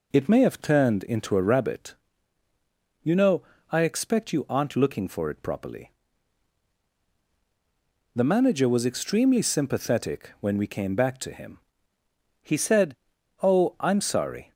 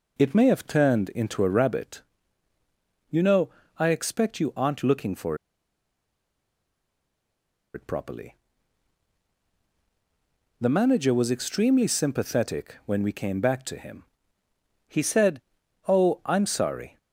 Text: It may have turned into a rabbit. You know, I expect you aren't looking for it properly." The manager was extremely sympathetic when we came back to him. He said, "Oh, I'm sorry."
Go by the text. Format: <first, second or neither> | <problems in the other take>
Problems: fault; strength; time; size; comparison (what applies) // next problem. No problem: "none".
first | pauses between "for" and "it"; strong; at 5.3 s; 2.3 s long